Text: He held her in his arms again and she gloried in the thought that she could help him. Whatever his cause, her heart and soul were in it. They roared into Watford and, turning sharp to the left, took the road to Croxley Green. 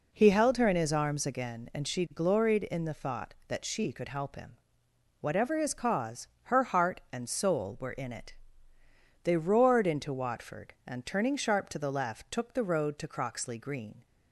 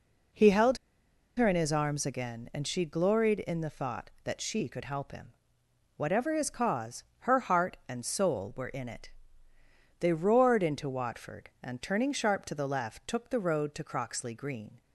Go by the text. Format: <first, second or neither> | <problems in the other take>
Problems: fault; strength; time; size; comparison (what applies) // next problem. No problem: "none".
first | pauses between "held" and "her"; noticeable; at 0.7 s; 0.60 s long